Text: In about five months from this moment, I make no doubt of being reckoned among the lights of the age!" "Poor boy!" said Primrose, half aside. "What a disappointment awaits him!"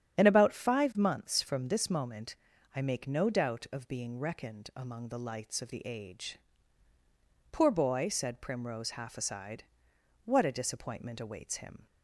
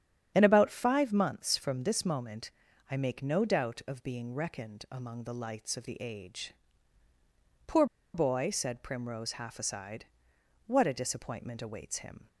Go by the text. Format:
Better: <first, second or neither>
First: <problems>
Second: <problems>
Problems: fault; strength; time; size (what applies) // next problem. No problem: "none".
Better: first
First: starts louder than the rest; strong; until 1.2 s; 8.5 dB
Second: starts louder than the rest; strong; until 1.3 s; 9 dB // pauses between "Poor" and "boy"; slight; at 7.8 s; 0.29 s long